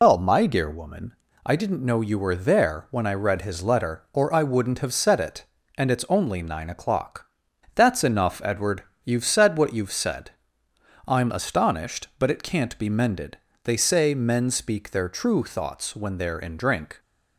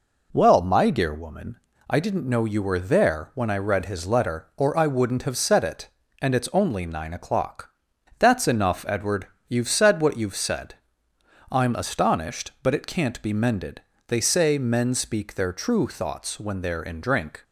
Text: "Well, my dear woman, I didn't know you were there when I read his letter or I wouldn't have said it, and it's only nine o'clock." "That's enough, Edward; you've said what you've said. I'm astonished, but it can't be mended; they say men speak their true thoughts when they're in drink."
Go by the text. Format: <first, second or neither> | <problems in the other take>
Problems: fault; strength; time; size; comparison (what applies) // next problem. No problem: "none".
second | loses the start of "Well"; at 0.0 s; 150 ms